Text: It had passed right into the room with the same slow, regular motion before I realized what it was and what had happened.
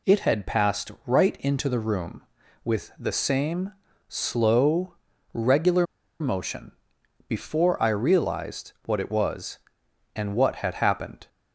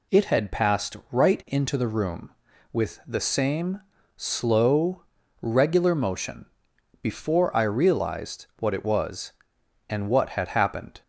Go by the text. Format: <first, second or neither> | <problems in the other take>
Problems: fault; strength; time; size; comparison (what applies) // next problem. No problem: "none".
second | pauses between "same" and "slow"; slight; at 3.7 s; 0.36 s long; slight in the second // pauses between "regular" and "motion"; slight; at 5.8 s; 0.34 s long // pauses between "motion" and "before"; noticeable; at 6.7 s; 0.56 s long; noticeable in the second